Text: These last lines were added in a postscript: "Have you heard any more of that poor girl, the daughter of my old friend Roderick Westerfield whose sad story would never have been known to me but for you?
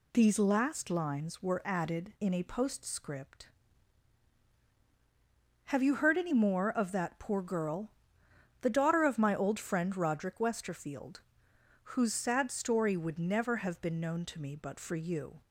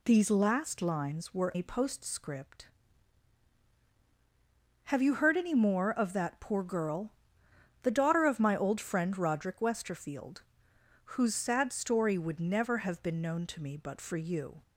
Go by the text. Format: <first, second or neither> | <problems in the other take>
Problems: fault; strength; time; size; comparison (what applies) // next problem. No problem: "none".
first | skips "added in"; at 1.5 s // pauses between "Westerfield" and "whose"; noticeable; at 10.4 s; 0.72 s long; noticeable in the first